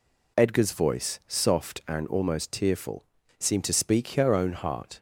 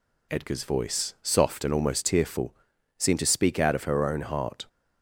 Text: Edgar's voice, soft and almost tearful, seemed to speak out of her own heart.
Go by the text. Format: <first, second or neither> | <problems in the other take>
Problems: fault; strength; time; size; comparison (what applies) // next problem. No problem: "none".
second | skips "out of"; at 4.0 s